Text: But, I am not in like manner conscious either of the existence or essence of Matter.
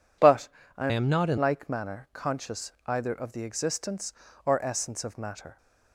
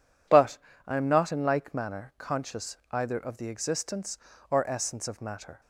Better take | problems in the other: second | changes voice from "am" to "in"; from 0.9 to 1.3 s; 0.4 s long

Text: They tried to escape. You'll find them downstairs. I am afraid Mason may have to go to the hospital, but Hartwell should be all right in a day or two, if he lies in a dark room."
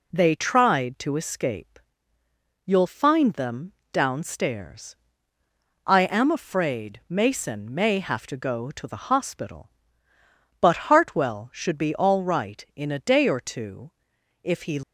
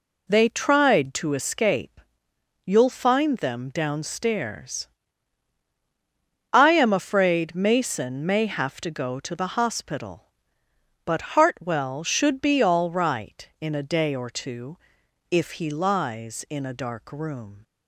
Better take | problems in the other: second | pauses between "them" and "downstairs"; slight; at 3.7 s; 0.20 s long // stops before "lies in a dark room"; at 14.8 s

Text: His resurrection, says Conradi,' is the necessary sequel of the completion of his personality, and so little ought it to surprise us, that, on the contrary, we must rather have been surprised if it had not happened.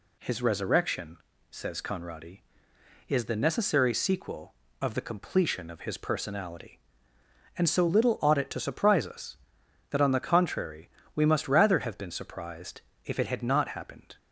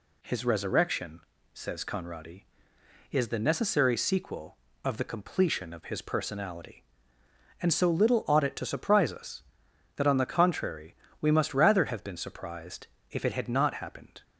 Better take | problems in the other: neither | pauses between "surprised" and "if"; slight; the same in both

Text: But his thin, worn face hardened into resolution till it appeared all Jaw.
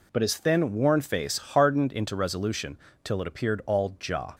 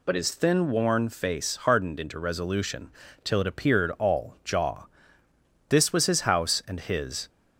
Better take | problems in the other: first | pauses between "resolution" and "till"; slight; at 2.9 s; 0.32 s long; slight in the first // goes on to say "This was his house and his"; from 5.6 s on; 1.6 s long

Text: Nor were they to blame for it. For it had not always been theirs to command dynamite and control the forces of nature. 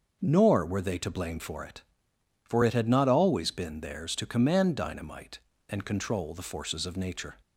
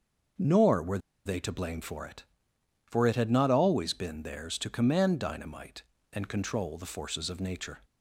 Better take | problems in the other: first | starts louder than the rest; until 1.6 s; 6.5 dB; also in the first // pauses between "were" and "they"; slight; at 0.9 s; 0.27 s long

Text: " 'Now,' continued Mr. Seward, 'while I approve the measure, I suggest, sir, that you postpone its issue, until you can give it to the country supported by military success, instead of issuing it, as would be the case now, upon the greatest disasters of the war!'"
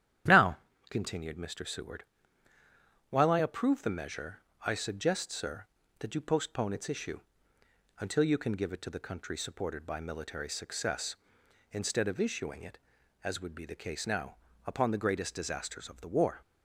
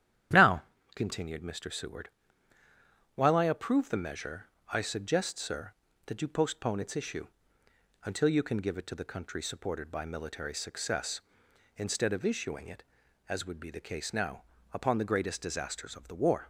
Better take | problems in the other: neither | starts louder than the rest; strong; the same in both

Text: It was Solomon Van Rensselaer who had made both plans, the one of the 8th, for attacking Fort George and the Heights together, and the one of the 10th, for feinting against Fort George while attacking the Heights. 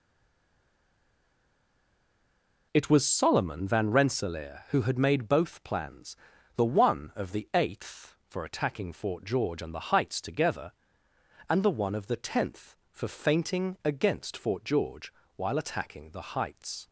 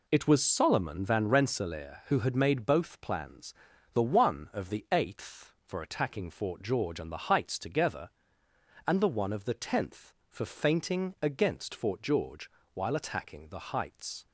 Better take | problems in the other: second | stays silent before the first word; strong; until 2.7 s; 2.7 s long // pauses between "George" and "while"; slight; at 15.1 s; 0.24 s long; slight in the second

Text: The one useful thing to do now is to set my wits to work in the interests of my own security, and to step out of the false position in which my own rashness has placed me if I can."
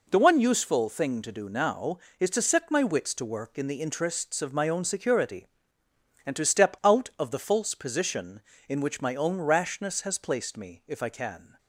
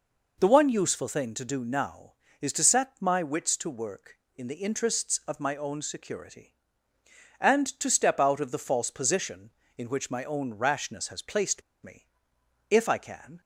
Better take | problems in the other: first | pauses between "placed" and "me"; slight; at 11.6 s; 0.22 s long // pauses between "me" and "if"; noticeable; at 12.0 s; 0.64 s long

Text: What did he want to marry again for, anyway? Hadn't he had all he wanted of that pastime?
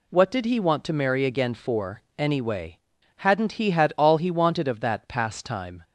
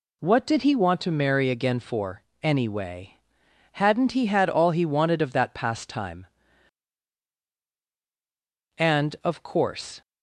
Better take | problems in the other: first | goes on to say "And of course"; noticeable; from 8.7 s on; 1.2 s long

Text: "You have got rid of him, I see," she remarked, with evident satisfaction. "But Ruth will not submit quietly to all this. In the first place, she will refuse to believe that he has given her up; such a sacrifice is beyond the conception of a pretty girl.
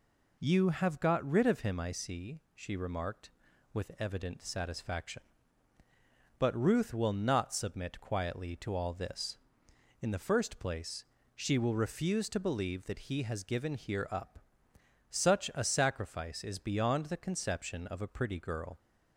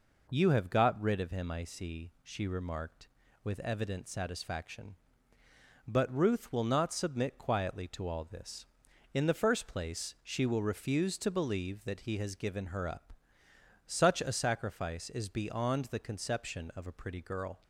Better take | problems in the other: second | says "here" for "her"; at 13.7 s

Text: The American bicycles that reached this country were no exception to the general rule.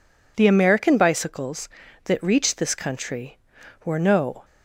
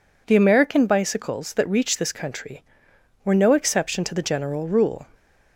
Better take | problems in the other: second | stops before "exception to the general rule"; at 4.4 s

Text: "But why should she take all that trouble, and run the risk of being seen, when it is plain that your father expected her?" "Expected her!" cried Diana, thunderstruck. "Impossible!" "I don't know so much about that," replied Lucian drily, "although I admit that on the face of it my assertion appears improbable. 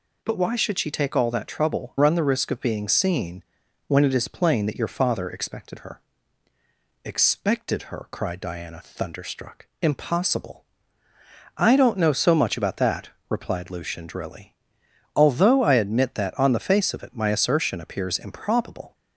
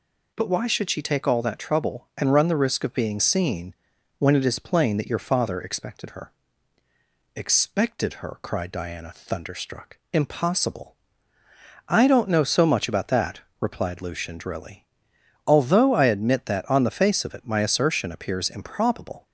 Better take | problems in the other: second | skips "and"; at 1.9 s

